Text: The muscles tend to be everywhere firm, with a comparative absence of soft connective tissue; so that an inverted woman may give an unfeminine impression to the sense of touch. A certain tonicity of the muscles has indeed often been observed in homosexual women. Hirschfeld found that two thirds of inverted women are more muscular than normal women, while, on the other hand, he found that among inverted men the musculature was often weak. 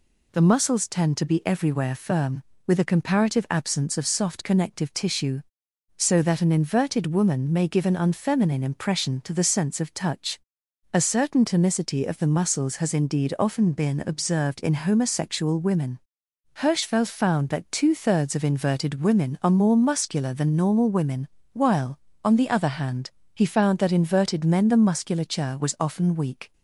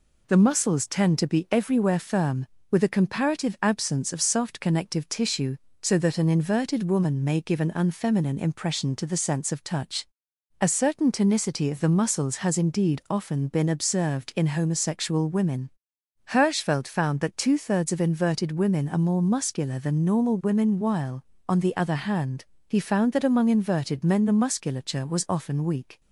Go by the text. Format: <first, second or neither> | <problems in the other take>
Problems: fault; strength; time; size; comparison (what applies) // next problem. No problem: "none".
second | skips "among"; at 23.9 s